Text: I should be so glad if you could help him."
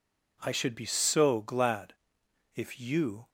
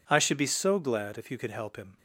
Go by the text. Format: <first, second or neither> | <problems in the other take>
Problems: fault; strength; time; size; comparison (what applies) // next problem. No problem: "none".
second | pauses between "glad" and "if"; noticeable; at 1.9 s; 0.62 s long // stops before "could help him"; at 3.2 s